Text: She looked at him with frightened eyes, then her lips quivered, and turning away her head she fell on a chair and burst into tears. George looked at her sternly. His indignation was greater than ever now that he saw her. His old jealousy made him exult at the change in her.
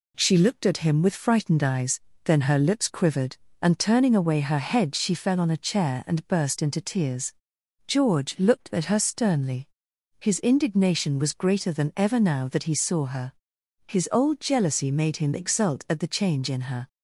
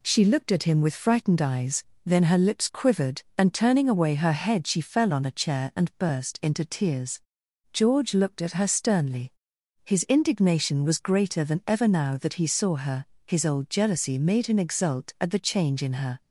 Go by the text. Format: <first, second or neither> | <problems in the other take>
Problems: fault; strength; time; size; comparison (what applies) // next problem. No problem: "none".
neither | none